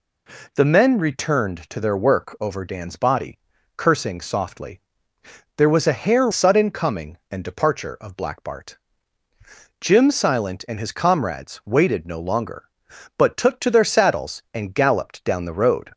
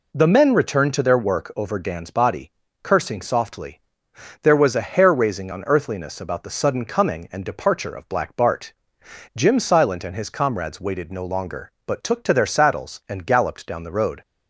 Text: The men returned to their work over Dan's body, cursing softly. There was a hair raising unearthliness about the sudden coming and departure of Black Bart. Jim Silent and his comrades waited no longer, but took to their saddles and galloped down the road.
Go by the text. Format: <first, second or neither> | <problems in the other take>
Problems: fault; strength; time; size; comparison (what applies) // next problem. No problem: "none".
second | skips "raising unearthliness about the"; at 6.3 s